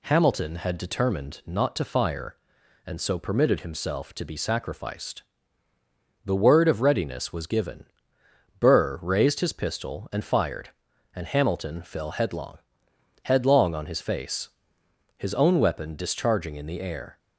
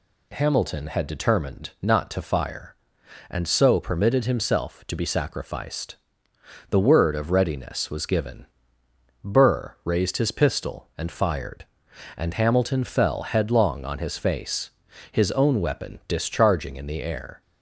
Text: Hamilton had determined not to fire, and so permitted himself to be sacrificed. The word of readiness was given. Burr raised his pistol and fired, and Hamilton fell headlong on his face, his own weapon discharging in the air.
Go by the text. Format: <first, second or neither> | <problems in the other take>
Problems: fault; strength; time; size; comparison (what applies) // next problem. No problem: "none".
second | says "headlong" twice; at 13.2 s